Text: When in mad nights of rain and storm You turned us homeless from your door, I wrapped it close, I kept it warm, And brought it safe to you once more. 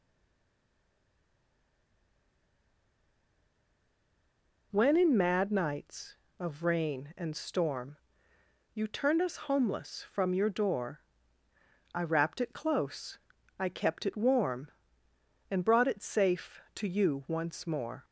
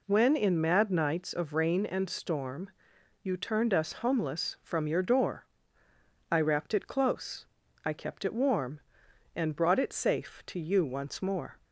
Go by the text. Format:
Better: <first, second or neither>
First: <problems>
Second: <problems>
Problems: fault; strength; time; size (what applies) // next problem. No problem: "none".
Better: second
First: stays silent before the first word; strong; until 4.7 s; 4.7 s long // pauses between "storm" and "You"; noticeable; at 7.9 s; 0.76 s long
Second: pauses between "storm" and "You"; noticeable; at 2.6 s; 0.54 s long